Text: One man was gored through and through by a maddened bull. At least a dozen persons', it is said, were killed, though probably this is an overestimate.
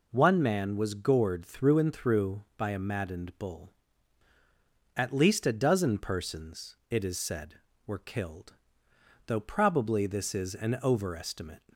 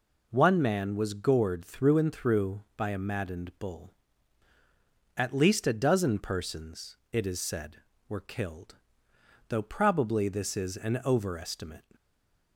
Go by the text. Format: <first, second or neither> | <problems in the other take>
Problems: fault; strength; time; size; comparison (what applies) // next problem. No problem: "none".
first | stays silent after the last word; slight; from 11.9 s on; 0.6 s long